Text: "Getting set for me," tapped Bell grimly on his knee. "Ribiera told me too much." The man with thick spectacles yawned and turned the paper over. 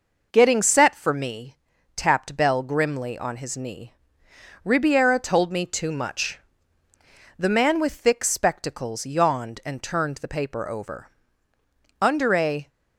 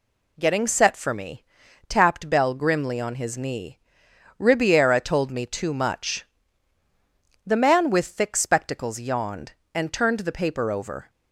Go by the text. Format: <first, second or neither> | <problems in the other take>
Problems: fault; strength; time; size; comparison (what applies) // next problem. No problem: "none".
second | goes on to say "Under a"; noticeable; from 12.0 s on; 0.68 s long